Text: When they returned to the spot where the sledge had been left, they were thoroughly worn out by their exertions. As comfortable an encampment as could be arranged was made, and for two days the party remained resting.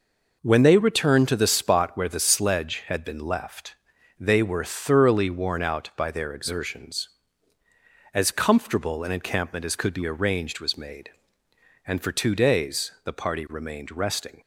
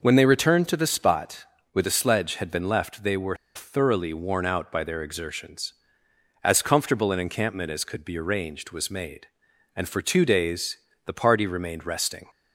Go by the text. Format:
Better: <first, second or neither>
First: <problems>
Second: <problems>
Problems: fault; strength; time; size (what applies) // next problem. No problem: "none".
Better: first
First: none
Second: pauses between "spot" and "where"; slight; at 1.4 s; 0.28 s long // pauses between "were" and "thoroughly"; slight; at 3.3 s; 0.20 s long // pauses between "days" and "the"; slight; at 10.7 s; 0.30 s long